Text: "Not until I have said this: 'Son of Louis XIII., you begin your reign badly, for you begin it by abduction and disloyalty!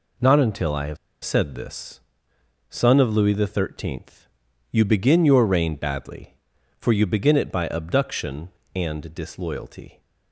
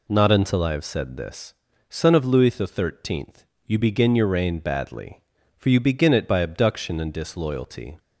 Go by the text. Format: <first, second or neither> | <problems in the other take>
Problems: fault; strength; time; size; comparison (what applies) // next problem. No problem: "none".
second | pauses between "have" and "said"; slight; at 0.9 s; 0.27 s long